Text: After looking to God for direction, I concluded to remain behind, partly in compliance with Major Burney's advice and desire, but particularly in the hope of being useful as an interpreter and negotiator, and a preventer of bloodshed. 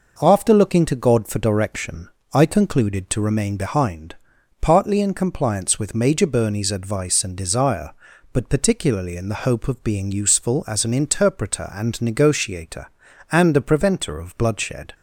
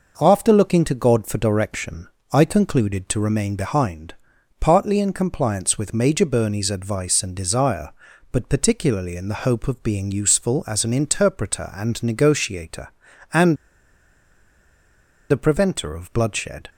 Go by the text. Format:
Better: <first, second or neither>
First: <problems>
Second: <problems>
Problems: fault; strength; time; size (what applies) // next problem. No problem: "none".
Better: first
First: none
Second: pauses between "and" and "a"; strong; at 13.5 s; 1.7 s long